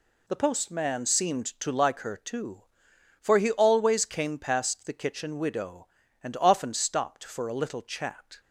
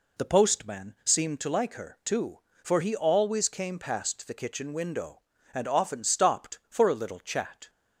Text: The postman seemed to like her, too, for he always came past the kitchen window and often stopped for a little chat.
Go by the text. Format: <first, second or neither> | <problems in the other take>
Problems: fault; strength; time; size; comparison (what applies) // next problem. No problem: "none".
second | says "widow" for "window"; at 5.3 s